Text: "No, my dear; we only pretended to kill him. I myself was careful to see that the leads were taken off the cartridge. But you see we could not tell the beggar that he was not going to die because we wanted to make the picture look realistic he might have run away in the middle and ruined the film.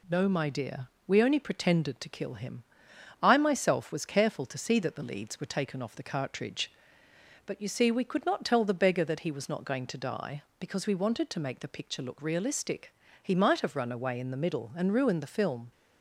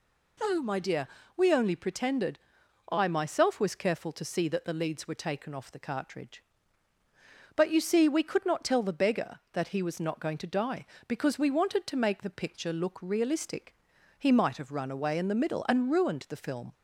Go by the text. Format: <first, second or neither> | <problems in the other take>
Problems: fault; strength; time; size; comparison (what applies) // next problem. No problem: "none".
first | skips "to kill him"; at 2.6 s // pauses between "realistic" and "he"; at 13.7 s; 0.44 s long; slight in the first